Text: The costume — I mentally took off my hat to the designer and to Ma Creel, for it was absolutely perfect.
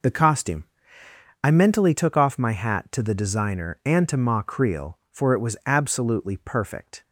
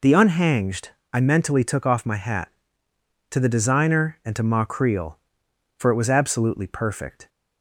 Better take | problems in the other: first | says "unhanged" for "costume"; at 0.1 s

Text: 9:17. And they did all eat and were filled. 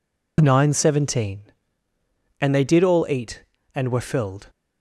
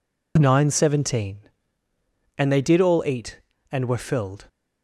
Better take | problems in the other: neither | none

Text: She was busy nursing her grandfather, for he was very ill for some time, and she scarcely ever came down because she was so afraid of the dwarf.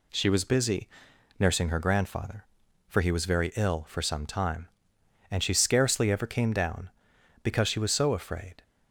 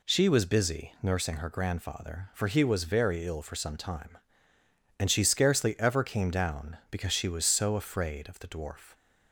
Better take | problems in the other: second | pauses between "busy" and "nursing"; noticeable; at 0.8 s; 0.50 s long // stops before "of the dwarf"; at 8.6 s

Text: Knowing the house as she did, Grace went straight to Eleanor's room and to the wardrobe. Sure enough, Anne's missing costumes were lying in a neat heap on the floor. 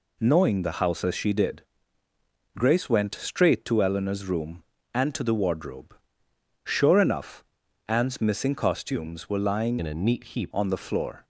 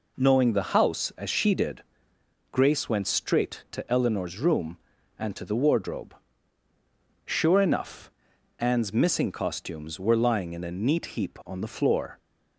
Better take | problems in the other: second | changes voice from "in" to "heap"; from 9.7 to 10.5 s; 0.8 s long

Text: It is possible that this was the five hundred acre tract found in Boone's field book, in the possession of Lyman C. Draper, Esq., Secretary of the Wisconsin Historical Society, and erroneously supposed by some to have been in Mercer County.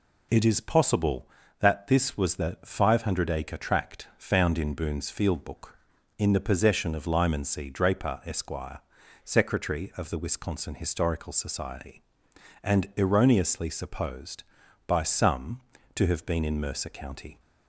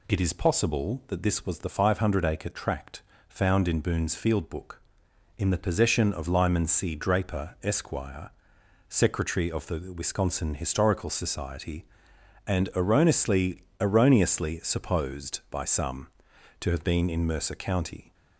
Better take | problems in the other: first | pauses between "tract" and "found"; slight; at 3.0 s; 0.28 s long // says "erroneously" twice; at 13.7 s

